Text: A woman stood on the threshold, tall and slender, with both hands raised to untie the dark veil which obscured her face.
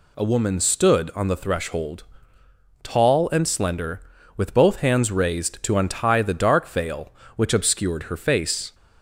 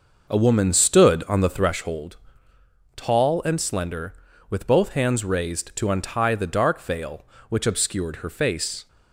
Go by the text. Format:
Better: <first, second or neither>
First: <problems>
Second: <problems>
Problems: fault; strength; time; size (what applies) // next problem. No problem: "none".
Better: first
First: none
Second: starts louder than the rest; noticeable; until 1.8 s; 6 dB